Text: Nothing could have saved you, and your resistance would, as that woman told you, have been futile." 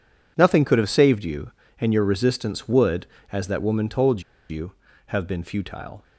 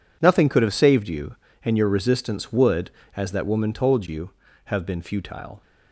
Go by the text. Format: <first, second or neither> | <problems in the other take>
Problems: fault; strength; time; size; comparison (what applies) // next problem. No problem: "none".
second | pauses between "told" and "you"; slight; at 4.2 s; 0.27 s long